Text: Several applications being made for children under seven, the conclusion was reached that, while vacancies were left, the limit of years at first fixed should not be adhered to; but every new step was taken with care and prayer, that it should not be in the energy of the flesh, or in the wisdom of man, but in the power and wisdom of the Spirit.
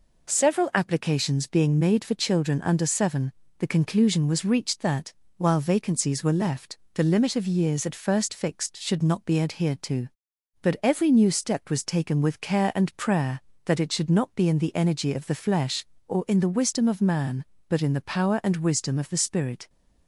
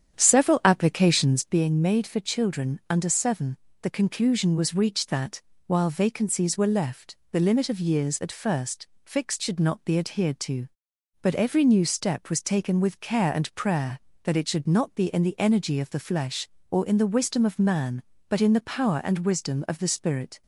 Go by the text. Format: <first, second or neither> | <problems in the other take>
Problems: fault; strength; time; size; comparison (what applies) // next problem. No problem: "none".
first | starts louder than the rest; strong; until 1.6 s; 9 dB // pauses between "first" and "fixed"; slight; at 8.8 s; 0.18 s long